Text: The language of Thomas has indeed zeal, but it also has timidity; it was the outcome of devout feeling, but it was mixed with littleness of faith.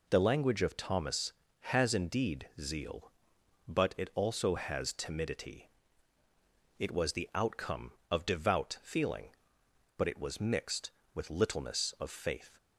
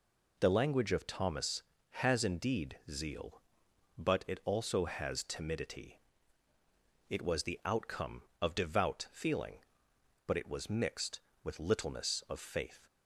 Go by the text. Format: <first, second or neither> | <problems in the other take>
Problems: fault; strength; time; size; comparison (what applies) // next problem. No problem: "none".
neither | none